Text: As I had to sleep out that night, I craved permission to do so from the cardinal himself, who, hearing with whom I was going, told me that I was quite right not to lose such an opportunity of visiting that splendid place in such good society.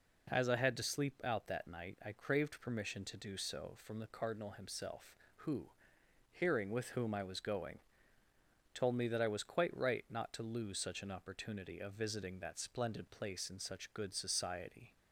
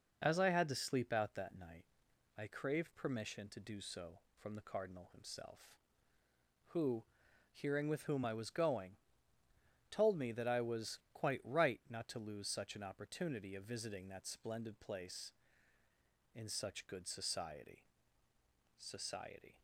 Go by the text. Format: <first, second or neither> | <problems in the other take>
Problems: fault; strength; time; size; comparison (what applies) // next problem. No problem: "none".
first | says "society" twice; at 18.7 s